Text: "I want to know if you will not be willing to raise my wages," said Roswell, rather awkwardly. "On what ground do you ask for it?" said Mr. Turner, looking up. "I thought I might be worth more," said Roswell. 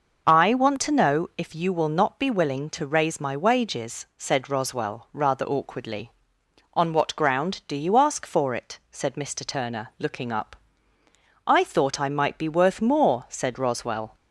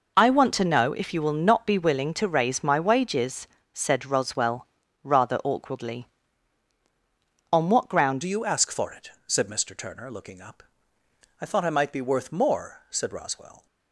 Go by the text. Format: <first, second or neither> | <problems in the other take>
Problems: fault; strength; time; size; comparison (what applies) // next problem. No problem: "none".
first | changes voice at "do"; from 8.2 s on; 5.4 s long